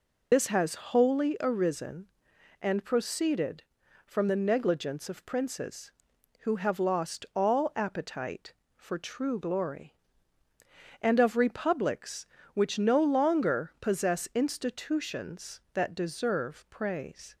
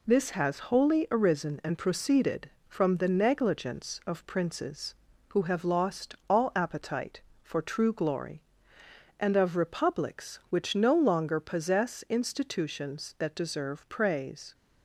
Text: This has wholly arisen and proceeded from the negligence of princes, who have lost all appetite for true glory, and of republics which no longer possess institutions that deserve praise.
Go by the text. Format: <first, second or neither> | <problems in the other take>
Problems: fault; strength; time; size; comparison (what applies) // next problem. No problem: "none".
second | loses the start of "This"; at 0.3 s; 55 ms